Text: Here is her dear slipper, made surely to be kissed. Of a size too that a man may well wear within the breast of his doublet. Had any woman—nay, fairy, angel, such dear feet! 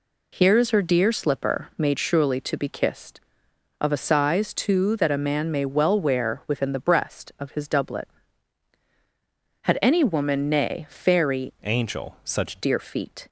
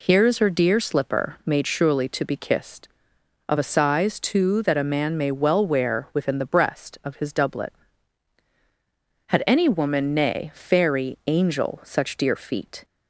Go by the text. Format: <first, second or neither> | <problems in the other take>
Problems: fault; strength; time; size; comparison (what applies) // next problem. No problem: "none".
second | changes voice from "angel" to "such"; from 11.6 to 12.5 s; 0.9 s long